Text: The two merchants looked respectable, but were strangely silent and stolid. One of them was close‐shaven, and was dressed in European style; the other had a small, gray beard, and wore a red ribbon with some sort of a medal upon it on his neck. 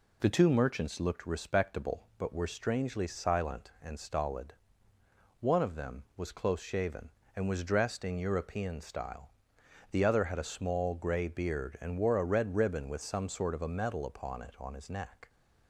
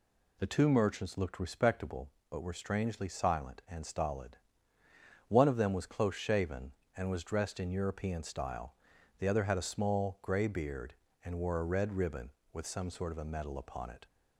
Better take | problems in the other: first | stops before "on his neck"; at 14.0 s

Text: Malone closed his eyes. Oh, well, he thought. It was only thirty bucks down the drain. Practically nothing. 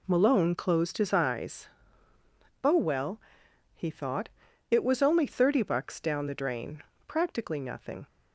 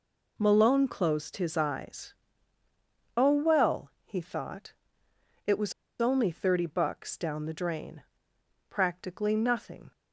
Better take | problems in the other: first | pauses between "was" and "only"; slight; at 5.7 s; 0.27 s long

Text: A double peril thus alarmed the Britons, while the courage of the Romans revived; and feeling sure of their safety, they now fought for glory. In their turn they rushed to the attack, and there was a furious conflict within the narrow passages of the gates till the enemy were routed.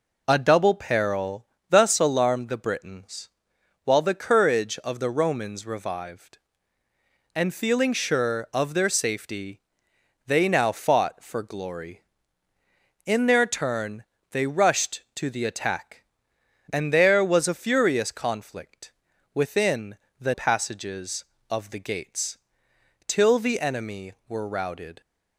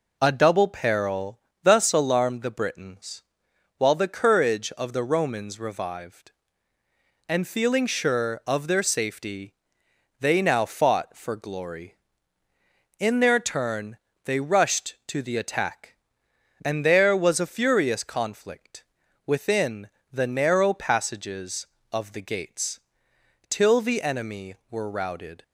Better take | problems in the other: second | pauses between "peril" and "thus"; slight; at 1.4 s; 0.24 s long; slight in the second // pauses between "turn" and "they"; slight; at 14.0 s; 0.28 s long; slight in the second // pauses between "conflict" and "within"; at 18.9 s; 0.42 s long; also in the second // pauses between "within" and "the"; slight; at 19.9 s; 0.20 s long; slight in the second // skips "narrow"; at 20.3 s // pauses between "gates" and "till"; noticeable; at 22.3 s; 0.70 s long; noticeable in the second

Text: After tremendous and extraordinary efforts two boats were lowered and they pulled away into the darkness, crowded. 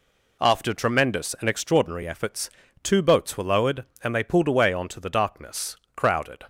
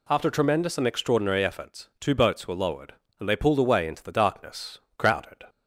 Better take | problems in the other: second | pauses between "efforts" and "two"; slight; at 2.4 s; 0.34 s long // says "onto" for "into"; at 4.7 s

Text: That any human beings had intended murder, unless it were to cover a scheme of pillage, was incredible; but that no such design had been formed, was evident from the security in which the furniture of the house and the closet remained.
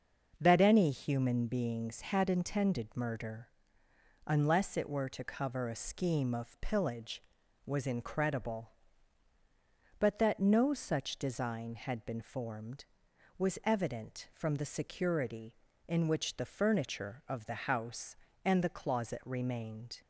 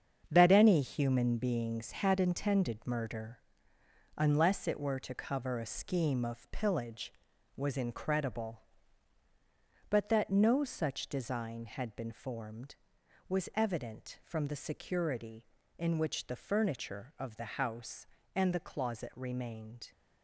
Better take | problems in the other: first | gets quieter; strong; throughout; 8.5 dB // starts louder than the rest; strong; until 1.3 s; 7 dB; noticeable in the first

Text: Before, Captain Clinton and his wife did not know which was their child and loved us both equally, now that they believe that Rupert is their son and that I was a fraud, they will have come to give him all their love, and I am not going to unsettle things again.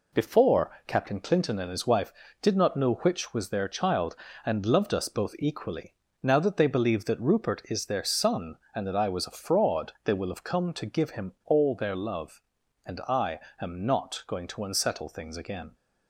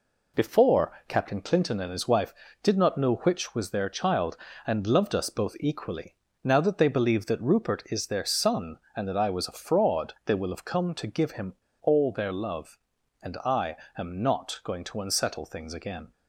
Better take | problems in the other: first | pauses between "him" and "all"; slight; at 11.5 s; 0.24 s long // pauses between "I" and "am"; slight; at 13.7 s; 0.20 s long; slight in the first

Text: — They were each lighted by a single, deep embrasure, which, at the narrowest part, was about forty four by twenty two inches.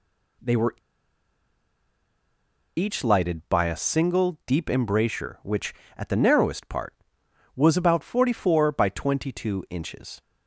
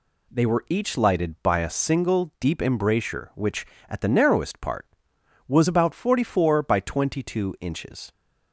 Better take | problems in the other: second | pauses between "were" and "each"; strong; at 0.7 s; 2.0 s long

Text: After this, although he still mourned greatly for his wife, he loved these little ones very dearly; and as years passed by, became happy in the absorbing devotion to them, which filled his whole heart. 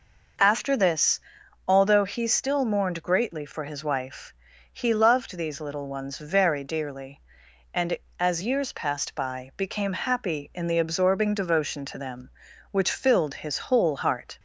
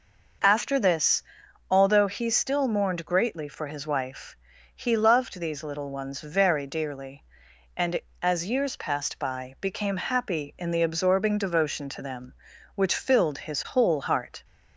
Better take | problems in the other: neither | none

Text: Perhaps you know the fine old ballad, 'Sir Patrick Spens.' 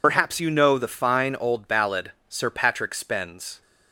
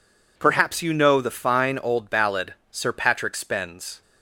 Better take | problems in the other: second | loses the start of "Perhaps"; at 0.0 s; 75 ms

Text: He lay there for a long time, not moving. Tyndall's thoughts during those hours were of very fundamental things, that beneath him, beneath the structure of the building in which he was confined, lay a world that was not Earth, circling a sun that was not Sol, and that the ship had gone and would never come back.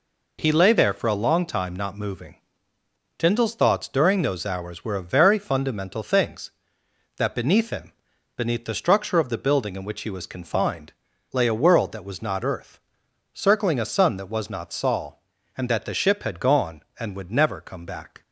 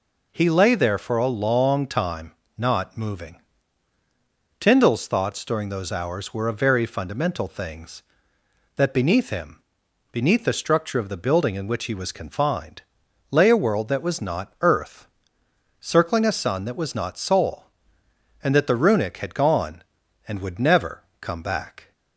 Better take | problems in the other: first | says "runic" for "ship"; at 18.7 s // pauses between "never" and "come"; slight; at 21.0 s; 0.16 s long

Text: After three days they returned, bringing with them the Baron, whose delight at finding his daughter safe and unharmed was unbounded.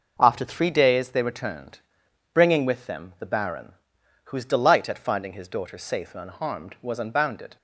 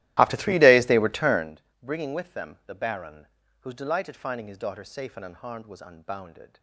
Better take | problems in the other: first | starts louder than the rest; strong; until 1.5 s; 15 dB

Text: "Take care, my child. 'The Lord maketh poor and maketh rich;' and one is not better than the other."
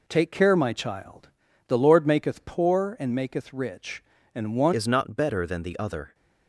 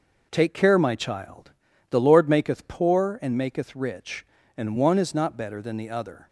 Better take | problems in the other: second | changes voice at "is"; from 4.7 s on; 1.4 s long

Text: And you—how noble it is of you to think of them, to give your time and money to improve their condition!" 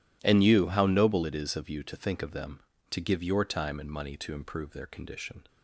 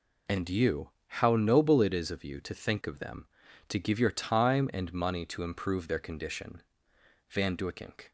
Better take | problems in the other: first | goes on to say "Van Duyckink"; noticeable; from 7.3 s on; 0.80 s long

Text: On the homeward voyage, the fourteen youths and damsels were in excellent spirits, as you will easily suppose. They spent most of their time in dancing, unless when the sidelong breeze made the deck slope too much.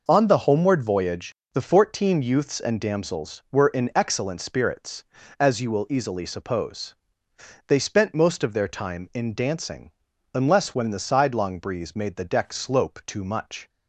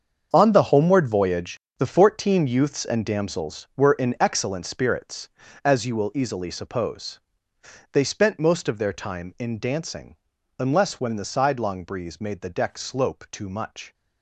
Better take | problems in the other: first | gets quieter; strong; throughout; 11.5 dB

